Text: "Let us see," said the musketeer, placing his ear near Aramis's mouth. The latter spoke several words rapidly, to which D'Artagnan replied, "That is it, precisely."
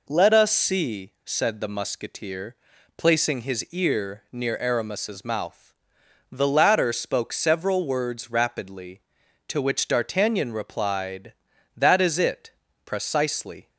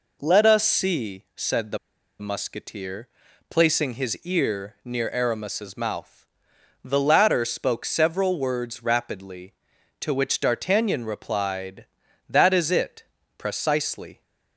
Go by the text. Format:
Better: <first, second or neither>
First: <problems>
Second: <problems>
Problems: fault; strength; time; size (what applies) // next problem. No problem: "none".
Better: first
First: none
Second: pauses between "the" and "musketeer"; at 1.7 s; 0.41 s long